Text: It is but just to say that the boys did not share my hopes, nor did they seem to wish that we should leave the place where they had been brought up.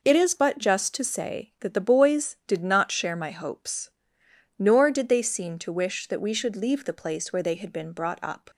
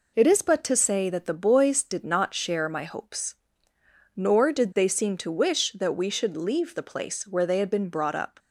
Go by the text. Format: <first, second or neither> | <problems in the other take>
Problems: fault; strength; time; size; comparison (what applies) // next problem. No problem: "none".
first | skips "just"; at 0.6 s